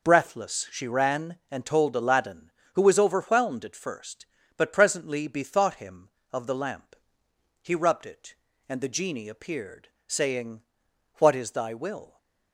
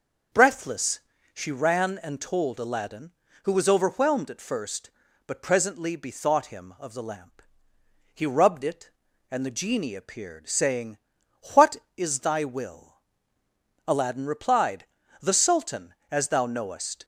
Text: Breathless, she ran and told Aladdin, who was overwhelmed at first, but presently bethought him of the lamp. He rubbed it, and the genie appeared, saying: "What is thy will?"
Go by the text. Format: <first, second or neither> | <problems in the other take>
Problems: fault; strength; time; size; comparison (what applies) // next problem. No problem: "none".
first | starts louder than the rest; noticeable; until 1.6 s; 6 dB // goes on to say "Aladdin replied The Sultan as thou knowest"; strong; from 13.8 s on; 3.1 s long